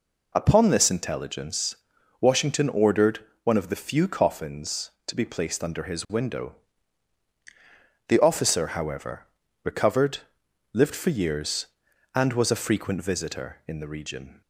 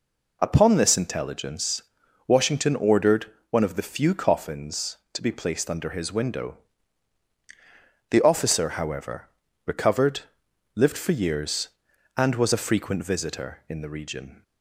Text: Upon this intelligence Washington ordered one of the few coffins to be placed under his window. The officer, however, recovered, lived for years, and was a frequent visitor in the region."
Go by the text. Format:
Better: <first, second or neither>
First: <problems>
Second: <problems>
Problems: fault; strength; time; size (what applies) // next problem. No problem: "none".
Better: neither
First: pauses between "intelligence" and "Washington"; at 1.7 s; 0.44 s long // pauses between "ordered" and "one"; slight; at 3.1 s; 0.24 s long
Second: pauses between "intelligence" and "Washington"; at 1.8 s; 0.44 s long // pauses between "ordered" and "one"; slight; at 3.2 s; 0.24 s long